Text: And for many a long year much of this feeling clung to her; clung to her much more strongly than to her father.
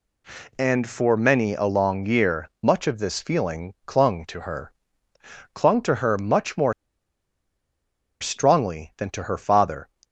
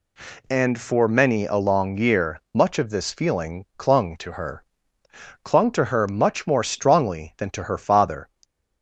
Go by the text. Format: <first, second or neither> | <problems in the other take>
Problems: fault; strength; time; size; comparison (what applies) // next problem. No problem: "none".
second | pauses between "more" and "strongly"; strong; at 6.7 s; 1.4 s long